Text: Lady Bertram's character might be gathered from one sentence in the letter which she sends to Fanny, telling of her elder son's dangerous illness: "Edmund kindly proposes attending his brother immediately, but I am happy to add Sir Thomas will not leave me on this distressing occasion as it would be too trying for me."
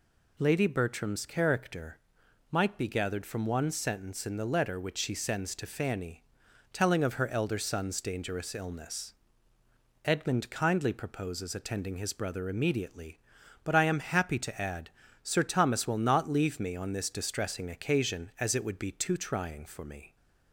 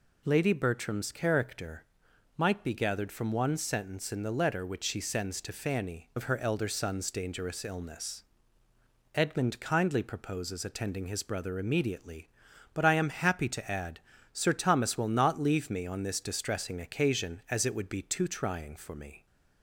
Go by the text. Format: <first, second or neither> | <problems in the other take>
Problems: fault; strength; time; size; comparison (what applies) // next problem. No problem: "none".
first | pauses between "character" and "might"; noticeable; at 1.8 s; 0.52 s long; noticeable in the first // skips "telling"; at 6.1 s // pauses between "add" and "Sir"; slight; at 13.9 s; 0.32 s long; slight in the first